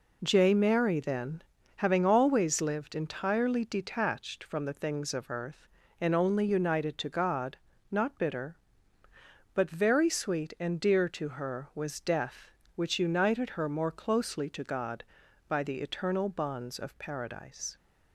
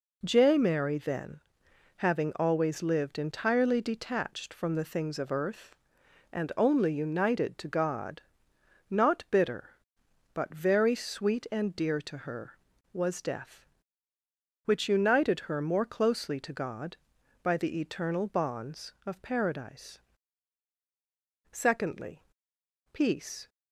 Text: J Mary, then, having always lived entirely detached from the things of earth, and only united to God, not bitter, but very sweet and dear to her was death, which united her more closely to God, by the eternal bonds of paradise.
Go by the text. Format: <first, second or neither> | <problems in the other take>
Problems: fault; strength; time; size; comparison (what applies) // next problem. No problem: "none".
first | goes on to say "Secondly peace"; strong; from 21.5 s on; 1.9 s long